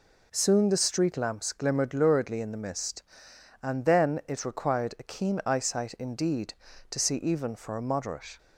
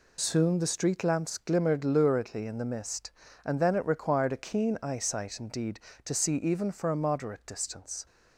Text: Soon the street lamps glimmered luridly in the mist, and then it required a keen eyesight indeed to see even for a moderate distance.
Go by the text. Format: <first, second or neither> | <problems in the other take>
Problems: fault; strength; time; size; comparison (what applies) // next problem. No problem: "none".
second | stops before "distance"; at 8.3 s